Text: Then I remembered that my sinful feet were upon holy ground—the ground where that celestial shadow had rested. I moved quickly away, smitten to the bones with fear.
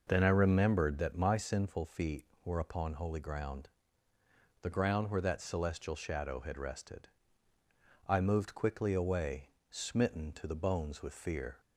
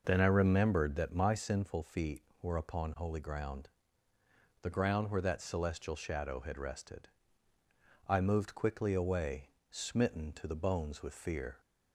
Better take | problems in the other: neither | none

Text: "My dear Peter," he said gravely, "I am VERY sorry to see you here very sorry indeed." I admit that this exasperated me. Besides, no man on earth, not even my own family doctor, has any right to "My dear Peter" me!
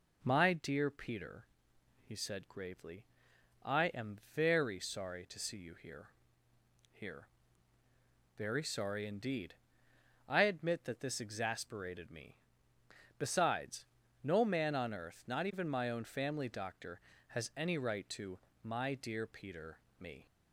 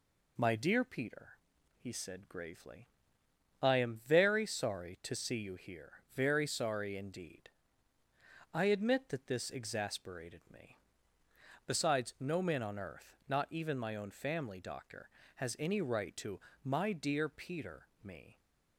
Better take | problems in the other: second | says "here" twice; at 6.9 s // pauses between "to" and "My"; slight; at 18.3 s; 0.22 s long; slight in the second // pauses between "Peter" and "me"; slight; at 19.7 s; 0.20 s long

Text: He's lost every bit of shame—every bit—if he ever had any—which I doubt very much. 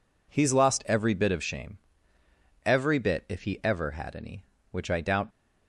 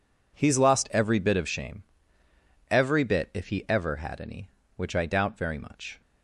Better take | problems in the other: second | stops before "very much"; at 5.3 s

